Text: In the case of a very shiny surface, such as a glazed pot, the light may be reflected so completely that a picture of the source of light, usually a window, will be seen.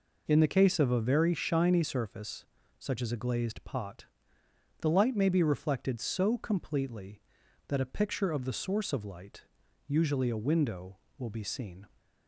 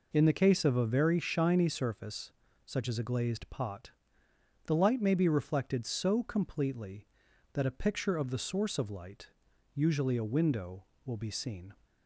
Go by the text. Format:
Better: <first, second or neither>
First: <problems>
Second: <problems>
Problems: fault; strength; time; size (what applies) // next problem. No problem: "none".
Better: neither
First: none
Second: none